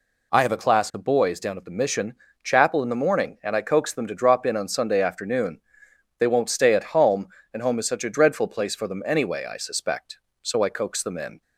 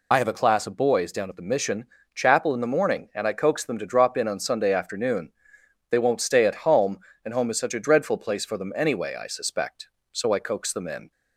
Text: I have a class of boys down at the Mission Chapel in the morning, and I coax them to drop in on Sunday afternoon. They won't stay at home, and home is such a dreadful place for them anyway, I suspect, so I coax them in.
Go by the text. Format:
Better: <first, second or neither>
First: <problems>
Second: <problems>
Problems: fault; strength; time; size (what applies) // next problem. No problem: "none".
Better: first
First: pauses between "Mission" and "Chapel"; slight; at 2.1 s; 0.28 s long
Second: loses the start of "I"; at 0.1 s; 35 ms // pauses between "Mission" and "Chapel"; slight; at 1.8 s; 0.28 s long